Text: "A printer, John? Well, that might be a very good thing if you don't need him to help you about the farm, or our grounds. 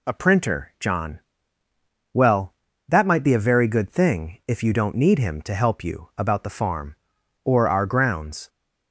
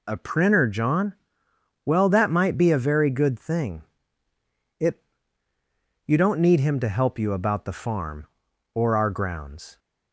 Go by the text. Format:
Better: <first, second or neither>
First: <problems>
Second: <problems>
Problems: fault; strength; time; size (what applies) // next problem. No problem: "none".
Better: first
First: none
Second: says "it" for "if"; at 4.7 s